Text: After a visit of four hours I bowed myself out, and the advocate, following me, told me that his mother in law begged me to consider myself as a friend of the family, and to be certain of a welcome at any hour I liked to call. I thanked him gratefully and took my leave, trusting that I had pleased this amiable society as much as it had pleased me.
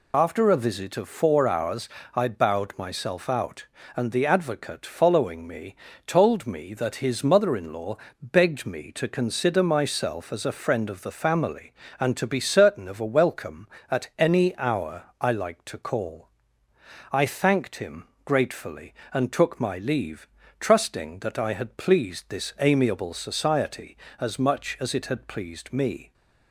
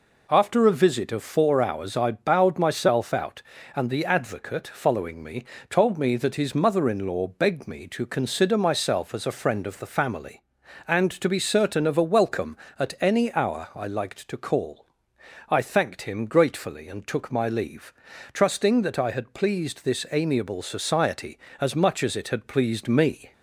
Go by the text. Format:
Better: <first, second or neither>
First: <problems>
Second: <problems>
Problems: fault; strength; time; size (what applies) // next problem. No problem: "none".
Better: second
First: loses the start of "After"; at 0.1 s; 30 ms // pauses between "hours" and "I"; slight; at 1.8 s; 0.28 s long // pauses between "law" and "begged"; slight; at 7.9 s; 0.24 s long // pauses between "hour" and "I"; slight; at 15.0 s; 0.18 s long // pauses between "him" and "gratefully"; slight; at 18.0 s; 0.20 s long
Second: none